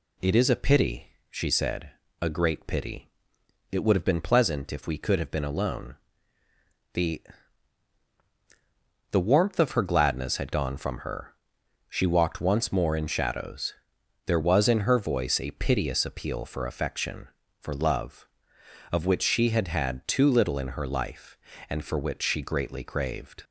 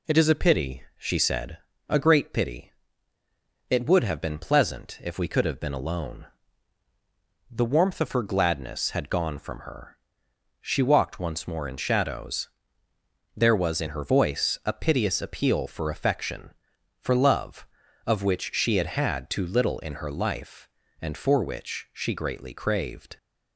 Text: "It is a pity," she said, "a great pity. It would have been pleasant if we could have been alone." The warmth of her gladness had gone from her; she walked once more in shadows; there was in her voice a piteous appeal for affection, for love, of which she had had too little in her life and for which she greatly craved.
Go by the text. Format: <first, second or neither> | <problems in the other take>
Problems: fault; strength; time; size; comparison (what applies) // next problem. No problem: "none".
second | says "The" twice; at 9.1 s